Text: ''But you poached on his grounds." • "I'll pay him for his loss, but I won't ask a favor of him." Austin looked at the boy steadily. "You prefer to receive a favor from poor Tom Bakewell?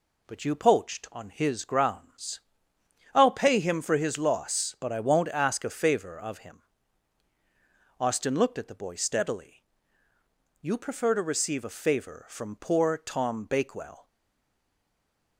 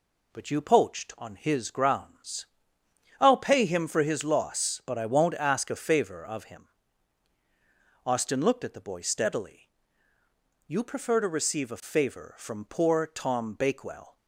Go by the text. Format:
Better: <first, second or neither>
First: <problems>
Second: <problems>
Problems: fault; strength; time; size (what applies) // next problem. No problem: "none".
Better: second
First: stays silent after the last word; noticeable; from 14.0 s on; 1.3 s long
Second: none